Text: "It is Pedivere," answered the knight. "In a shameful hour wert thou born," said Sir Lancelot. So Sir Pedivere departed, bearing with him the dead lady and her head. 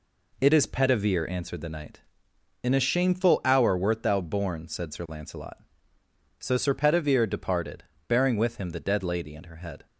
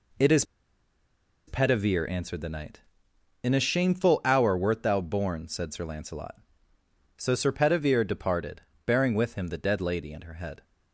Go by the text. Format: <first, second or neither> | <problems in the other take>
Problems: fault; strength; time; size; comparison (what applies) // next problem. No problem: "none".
first | pauses between "is" and "Pedivere"; at 0.4 s; 1.0 s long